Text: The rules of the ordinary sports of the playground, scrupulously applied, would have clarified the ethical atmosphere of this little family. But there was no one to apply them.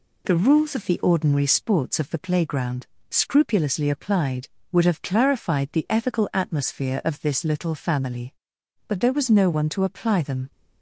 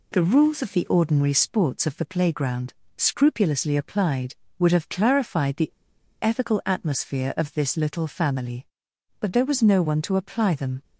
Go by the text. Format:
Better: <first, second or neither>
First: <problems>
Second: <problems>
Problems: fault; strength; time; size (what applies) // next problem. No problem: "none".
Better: first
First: none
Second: pauses between "the" and "ethical"; noticeable; at 5.7 s; 0.50 s long